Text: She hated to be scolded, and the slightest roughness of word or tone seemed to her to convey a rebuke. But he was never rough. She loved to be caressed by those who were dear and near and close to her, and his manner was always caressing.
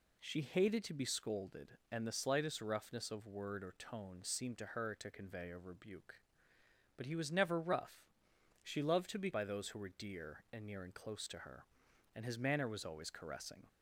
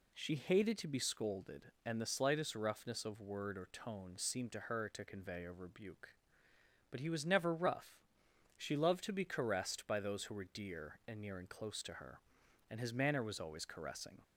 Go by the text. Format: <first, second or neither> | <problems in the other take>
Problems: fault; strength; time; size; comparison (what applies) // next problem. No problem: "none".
second | skips "caressed"; at 9.3 s